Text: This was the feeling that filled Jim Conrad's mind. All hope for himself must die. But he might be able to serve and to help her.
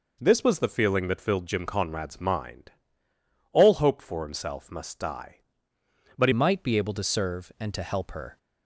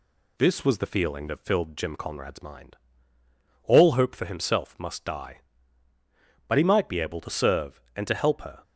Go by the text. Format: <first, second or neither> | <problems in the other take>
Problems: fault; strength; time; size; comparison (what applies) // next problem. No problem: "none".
second | changes voice at "might"; from 6.3 s on; 2.0 s long